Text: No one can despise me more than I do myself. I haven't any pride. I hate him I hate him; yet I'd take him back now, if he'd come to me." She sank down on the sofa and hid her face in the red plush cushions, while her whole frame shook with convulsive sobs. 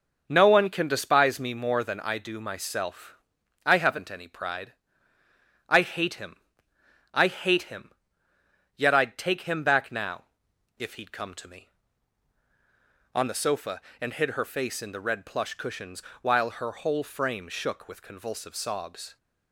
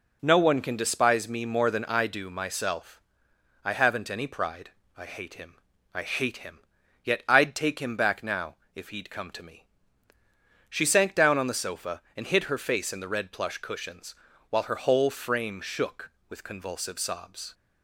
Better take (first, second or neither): second